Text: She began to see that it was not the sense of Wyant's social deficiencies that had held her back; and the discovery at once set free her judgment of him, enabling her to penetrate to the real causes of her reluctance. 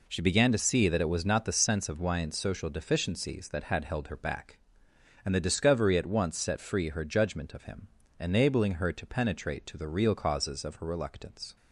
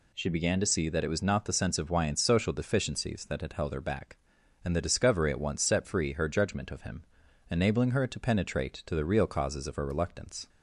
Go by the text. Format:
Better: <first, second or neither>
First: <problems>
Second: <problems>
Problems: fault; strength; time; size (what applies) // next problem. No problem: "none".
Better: neither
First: none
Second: none